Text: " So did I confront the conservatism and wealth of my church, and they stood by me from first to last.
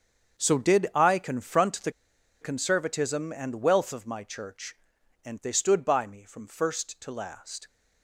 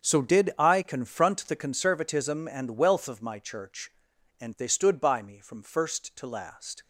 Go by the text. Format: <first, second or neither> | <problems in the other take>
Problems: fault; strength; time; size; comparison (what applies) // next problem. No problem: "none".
second | starts louder than the rest; strong; until 1.4 s; 7.5 dB; strong in the second // pauses between "the" and "conservatism"; noticeable; at 1.8 s; 0.51 s long